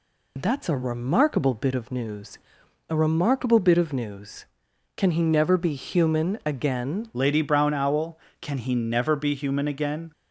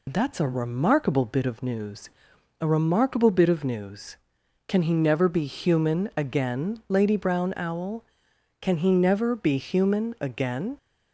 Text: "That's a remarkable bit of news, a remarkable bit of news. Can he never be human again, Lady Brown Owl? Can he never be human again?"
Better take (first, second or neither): second